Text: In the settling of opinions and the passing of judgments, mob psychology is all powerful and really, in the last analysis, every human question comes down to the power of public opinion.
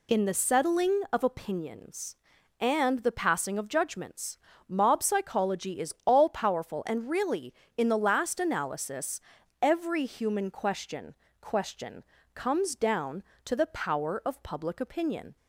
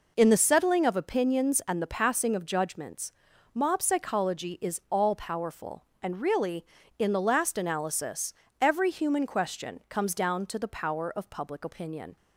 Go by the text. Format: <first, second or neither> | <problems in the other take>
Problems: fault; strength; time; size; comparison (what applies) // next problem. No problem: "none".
second | says "question" twice; at 11.3 s